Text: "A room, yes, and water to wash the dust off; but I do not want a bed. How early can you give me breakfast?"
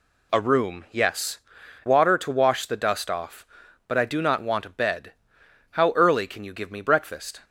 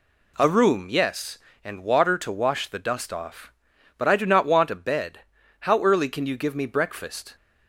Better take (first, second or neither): second